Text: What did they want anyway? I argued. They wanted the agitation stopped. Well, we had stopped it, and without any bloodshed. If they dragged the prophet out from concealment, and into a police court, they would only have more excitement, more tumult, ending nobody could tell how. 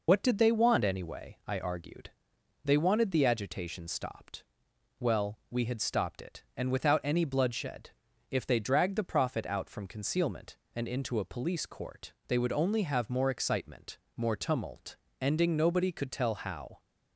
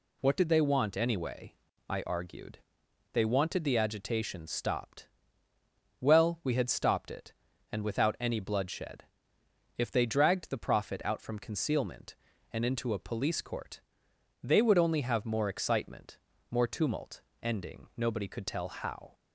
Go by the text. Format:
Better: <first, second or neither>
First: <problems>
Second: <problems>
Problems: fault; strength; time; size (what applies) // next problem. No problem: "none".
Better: second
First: loses the start of "What"; at 0.0 s; 45 ms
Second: none